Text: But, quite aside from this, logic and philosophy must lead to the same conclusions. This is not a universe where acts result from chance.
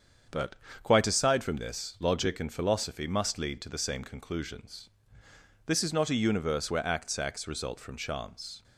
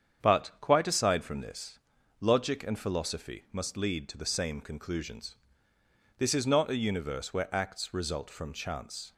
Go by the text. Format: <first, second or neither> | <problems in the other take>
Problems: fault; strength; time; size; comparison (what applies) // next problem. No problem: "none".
second | starts louder than the rest; strong; until 1.5 s; 7 dB; strong in the second // says "acts" twice; at 7.1 s